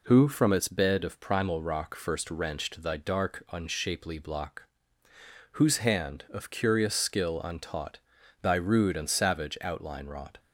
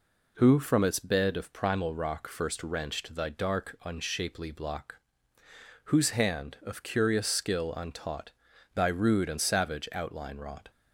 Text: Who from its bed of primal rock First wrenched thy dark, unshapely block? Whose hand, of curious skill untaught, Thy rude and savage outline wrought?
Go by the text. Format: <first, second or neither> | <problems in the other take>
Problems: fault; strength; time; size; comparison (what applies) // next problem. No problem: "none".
neither | none